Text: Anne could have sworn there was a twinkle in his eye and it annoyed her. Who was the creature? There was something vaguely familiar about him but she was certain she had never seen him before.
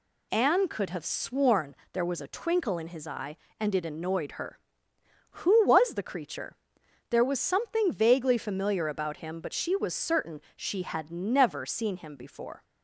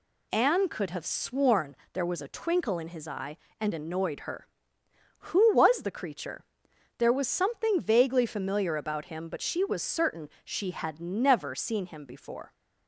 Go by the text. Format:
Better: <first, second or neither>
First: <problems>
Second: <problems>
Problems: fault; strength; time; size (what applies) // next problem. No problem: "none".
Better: first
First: pauses between "sworn" and "there"; slight; at 1.7 s; 0.18 s long // pauses between "certain" and "she"; slight; at 10.4 s; 0.16 s long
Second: pauses between "sworn" and "there"; slight; at 1.7 s; 0.18 s long // skips "it"; at 3.7 s // pauses between "certain" and "she"; slight; at 10.2 s; 0.16 s long